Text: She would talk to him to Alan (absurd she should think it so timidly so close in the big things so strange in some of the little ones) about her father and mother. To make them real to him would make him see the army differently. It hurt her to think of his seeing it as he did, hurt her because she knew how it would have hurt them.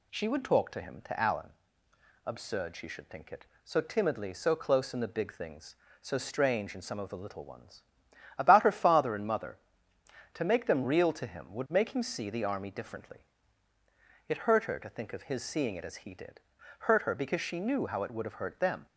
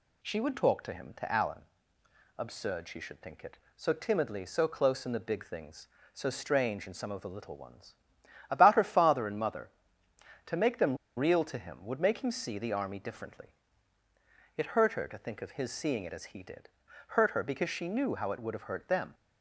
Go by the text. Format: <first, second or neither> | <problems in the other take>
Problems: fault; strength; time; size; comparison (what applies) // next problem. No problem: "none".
first | pauses between "them" and "real"; slight; at 10.9 s; 0.20 s long